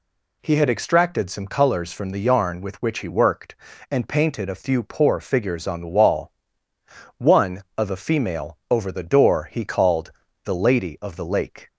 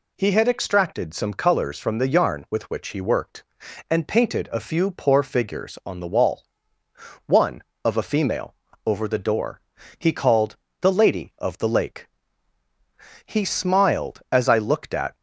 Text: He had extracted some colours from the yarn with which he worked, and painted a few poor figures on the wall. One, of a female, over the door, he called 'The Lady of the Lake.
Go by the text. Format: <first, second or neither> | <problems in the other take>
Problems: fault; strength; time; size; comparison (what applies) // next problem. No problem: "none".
first | pauses between "called" and "The"; slight; at 10.5 s; 0.24 s long; slight in the first // goes on to say "He smiled as I looked at"; strong; from 13.2 s on; 1.8 s long